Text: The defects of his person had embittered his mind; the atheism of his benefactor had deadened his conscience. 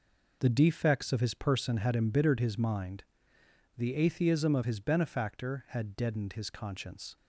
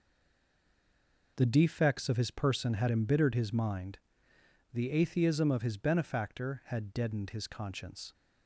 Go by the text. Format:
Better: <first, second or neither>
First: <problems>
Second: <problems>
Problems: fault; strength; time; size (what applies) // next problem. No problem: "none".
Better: first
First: none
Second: stays silent before the first word; noticeable; until 1.3 s; 1.3 s long